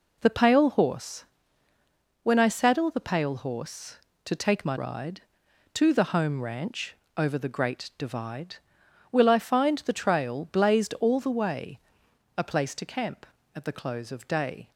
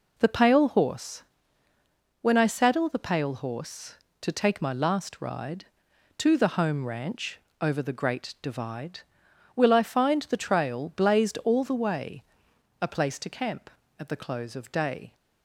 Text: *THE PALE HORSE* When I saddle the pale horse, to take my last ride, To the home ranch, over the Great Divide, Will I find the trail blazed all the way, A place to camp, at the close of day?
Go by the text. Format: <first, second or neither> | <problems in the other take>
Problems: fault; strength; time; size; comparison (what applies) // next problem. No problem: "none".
second | pauses between "HORSE" and "When"; noticeable; at 1.2 s; 0.98 s long; noticeable in the second // skips "last"; at 4.7 s